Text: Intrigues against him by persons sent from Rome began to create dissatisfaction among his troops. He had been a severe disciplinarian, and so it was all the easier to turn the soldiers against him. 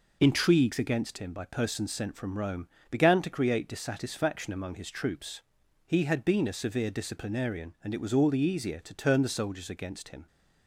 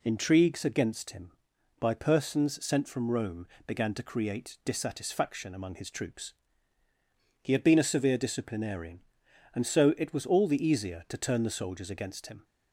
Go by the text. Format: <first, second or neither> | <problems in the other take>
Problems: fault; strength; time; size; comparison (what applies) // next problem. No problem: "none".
second | pauses between "Rome" and "began"; slight; at 2.6 s; 0.20 s long; slight in the second // skips "so"; at 7.9 s